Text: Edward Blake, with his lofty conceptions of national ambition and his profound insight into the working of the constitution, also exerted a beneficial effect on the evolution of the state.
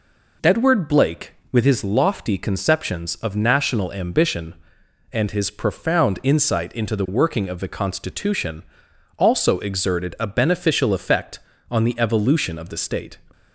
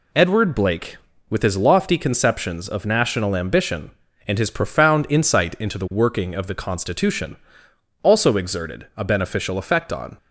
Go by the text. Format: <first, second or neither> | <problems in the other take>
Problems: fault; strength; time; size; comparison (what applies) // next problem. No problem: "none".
first | stops before "the evolution of the state"; at 10.1 s